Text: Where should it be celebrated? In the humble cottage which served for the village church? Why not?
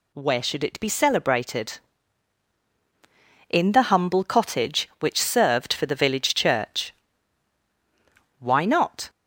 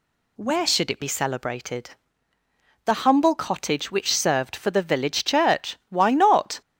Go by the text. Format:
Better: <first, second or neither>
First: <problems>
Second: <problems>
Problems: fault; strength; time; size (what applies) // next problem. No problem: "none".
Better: first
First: none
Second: skips "In"; at 2.3 s